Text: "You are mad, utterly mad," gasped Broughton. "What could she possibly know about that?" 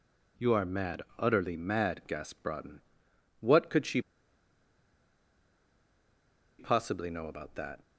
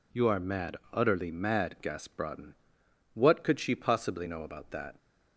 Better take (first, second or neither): second